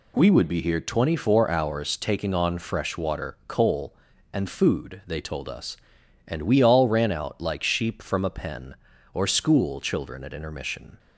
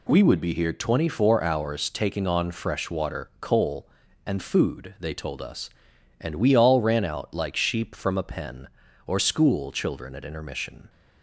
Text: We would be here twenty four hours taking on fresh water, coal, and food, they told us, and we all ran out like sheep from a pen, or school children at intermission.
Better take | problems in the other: neither | none

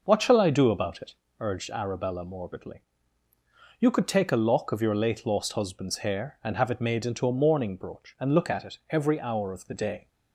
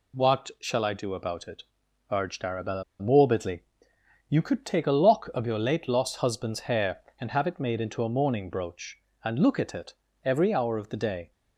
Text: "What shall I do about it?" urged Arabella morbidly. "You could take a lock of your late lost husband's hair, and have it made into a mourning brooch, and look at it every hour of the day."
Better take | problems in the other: first | pauses between "Arabella" and "morbidly"; slight; at 2.8 s; 0.17 s long // pauses between "it" and "every"; slight; at 9.9 s; 0.30 s long

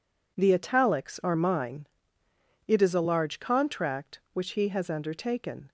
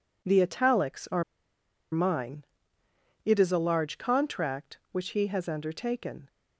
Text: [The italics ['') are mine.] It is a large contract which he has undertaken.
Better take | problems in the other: first | pauses between "are" and "mine"; noticeable; at 1.2 s; 0.70 s long

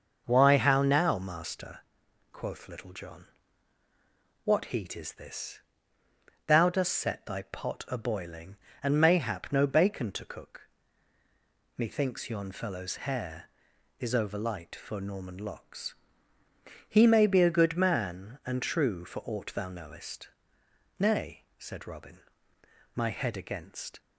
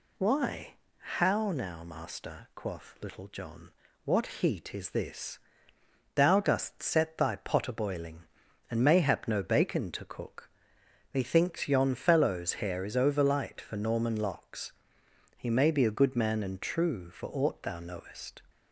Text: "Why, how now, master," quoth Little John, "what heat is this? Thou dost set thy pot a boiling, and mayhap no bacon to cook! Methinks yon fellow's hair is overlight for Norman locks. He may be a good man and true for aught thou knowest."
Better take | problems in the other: second | starts louder than the rest; noticeable; until 1.2 s; 6 dB // goes on to say "Nay said Robin my head against"; strong; from 20.9 s on; 3.0 s long

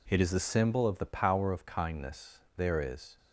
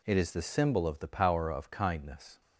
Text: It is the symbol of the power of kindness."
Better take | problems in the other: second | goes on to say "There is"; from 2.5 s on; 0.60 s long

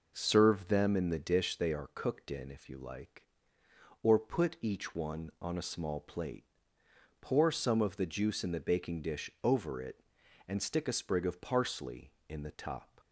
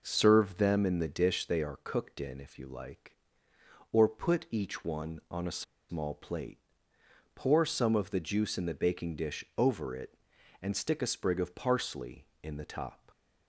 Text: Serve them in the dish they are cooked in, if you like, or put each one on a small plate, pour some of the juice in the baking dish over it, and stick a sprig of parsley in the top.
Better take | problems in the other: first | pauses between "a" and "small"; slight; at 5.6 s; 0.27 s long

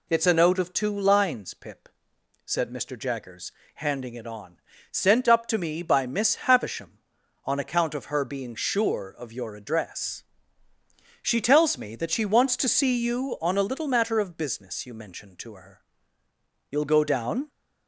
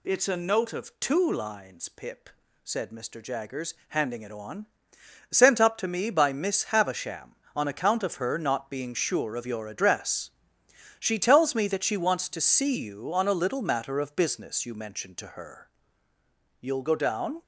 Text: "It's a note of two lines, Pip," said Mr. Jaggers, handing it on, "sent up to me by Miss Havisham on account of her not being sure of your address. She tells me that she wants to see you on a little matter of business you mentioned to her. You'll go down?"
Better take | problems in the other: second | skips "not"; at 8.2 s

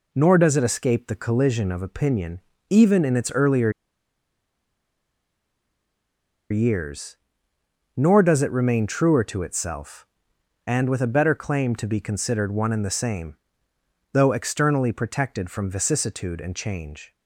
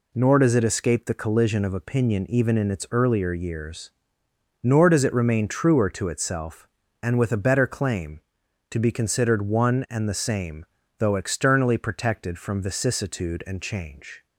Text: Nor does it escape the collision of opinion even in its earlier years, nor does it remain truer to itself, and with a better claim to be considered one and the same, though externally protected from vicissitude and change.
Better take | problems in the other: second | pauses between "opinion" and "even"; slight; at 2.4 s; 0.28 s long // pauses between "earlier" and "years"; strong; at 3.7 s; 2.7 s long

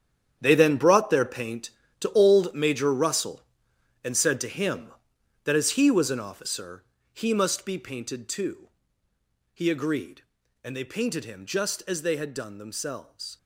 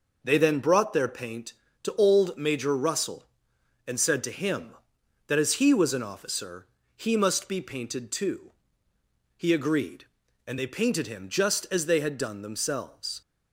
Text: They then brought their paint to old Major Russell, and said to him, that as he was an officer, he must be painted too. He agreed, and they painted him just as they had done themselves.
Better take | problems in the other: second | gets quieter; strong; throughout; 13 dB

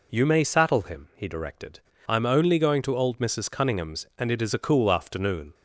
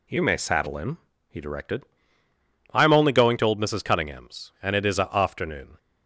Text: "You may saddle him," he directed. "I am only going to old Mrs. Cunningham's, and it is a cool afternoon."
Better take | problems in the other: first | skips "cool"; at 5.1 s

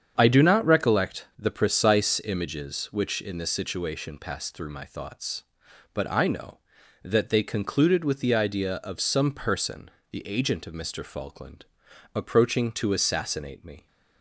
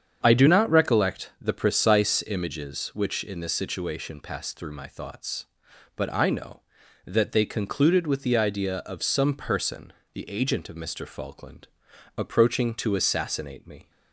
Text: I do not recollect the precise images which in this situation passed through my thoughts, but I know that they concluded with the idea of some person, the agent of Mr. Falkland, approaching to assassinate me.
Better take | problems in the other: neither | starts louder than the rest; strong; the same in both

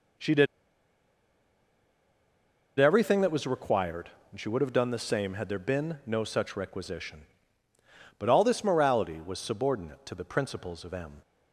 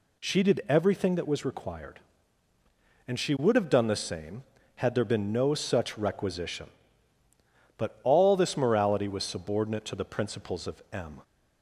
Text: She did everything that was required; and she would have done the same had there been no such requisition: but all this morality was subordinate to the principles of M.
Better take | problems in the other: second | pauses between "did" and "everything"; strong; at 0.4 s; 2.3 s long

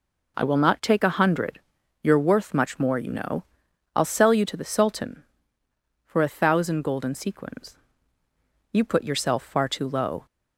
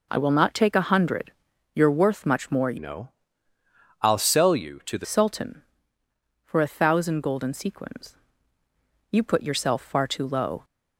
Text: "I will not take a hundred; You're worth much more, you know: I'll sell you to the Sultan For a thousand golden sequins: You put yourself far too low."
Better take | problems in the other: first | changes voice from "know" to "the"; from 2.7 to 5.0 s; 2.3 s long

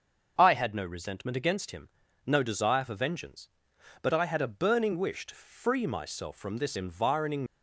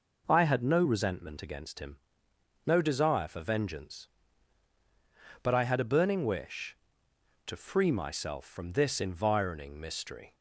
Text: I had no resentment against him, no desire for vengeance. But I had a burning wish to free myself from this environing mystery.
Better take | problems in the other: second | starts louder than the rest; until 1.3 s; 6.5 dB // stops before "mystery"; at 7.4 s

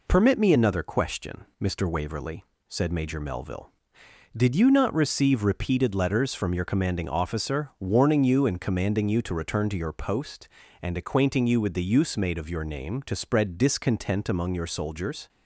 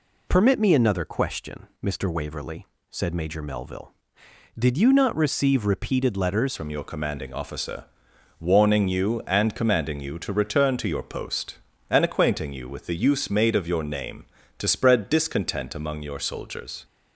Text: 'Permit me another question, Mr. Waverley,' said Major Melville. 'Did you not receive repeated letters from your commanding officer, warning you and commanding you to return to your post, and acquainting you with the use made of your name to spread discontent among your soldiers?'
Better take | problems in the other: first | changes voice at "from"; from 6.5 s on; 10.3 s long

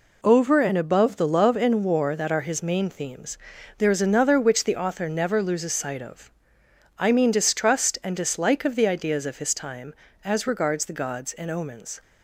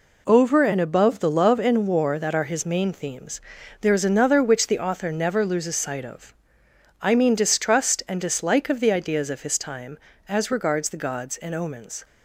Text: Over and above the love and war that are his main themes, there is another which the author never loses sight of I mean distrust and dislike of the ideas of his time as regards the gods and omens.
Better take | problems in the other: neither | pauses between "of" and "I"; noticeable; the same in both

